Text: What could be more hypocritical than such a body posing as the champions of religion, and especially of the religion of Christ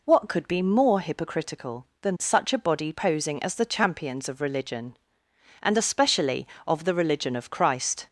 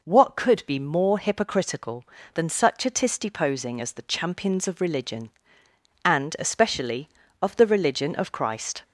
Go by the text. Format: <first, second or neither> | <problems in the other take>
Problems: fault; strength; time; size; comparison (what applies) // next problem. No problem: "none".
first | says "tisty" for "body"; at 2.8 s